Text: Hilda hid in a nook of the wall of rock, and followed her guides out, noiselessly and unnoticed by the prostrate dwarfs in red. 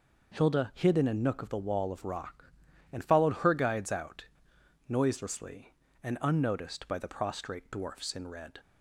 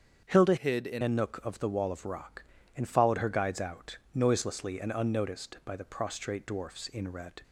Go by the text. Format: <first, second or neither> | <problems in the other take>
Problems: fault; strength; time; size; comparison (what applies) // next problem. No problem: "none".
first | starts louder than the rest; until 1.2 s; 7 dB // changes voice from "hid" to "in"; from 0.5 to 1.0 s; 0.5 s long